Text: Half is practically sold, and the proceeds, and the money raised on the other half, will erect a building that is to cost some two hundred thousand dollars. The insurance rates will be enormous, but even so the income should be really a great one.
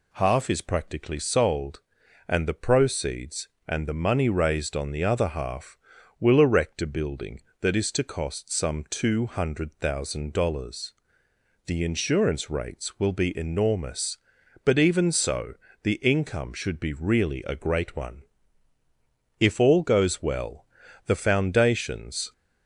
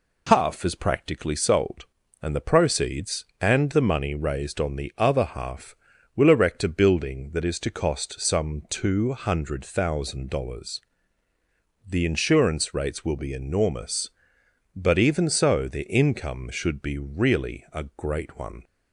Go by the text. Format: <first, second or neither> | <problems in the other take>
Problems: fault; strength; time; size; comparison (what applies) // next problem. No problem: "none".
second | pauses between "so" and "the"; slight; at 15.5 s; 0.30 s long // goes on to say "If all goes well the foundations"; strong; from 19.4 s on; 2.9 s long